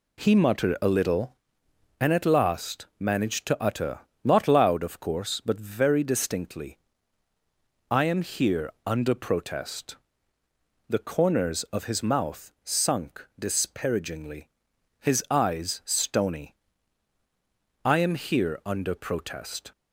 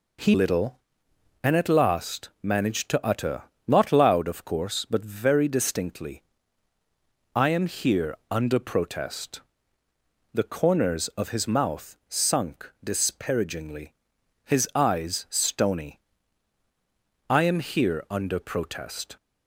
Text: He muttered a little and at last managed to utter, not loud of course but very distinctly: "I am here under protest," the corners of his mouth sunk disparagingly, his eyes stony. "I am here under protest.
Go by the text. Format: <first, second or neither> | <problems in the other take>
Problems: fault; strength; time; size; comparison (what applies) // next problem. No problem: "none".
first | skips "muttered a"; at 0.3 s